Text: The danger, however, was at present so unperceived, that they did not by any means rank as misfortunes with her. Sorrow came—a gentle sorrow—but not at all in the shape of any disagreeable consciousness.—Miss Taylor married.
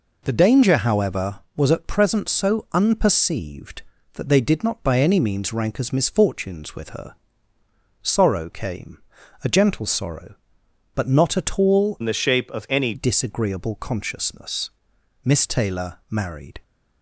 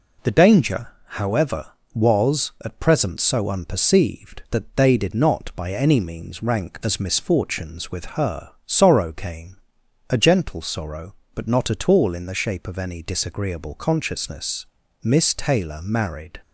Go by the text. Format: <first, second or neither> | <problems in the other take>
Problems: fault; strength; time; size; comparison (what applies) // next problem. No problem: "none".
second | changes voice from "in" to "any"; from 12.0 to 12.9 s; 0.9 s long